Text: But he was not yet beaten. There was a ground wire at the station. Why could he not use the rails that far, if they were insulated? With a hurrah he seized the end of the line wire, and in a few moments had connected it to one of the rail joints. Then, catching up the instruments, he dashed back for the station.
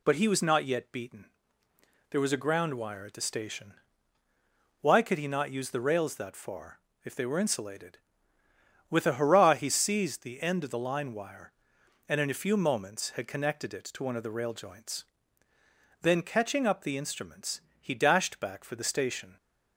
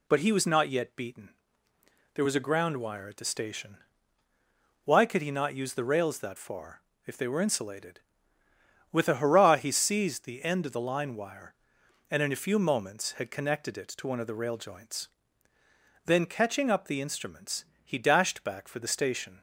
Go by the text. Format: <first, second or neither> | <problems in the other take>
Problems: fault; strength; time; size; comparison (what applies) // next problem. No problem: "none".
neither | none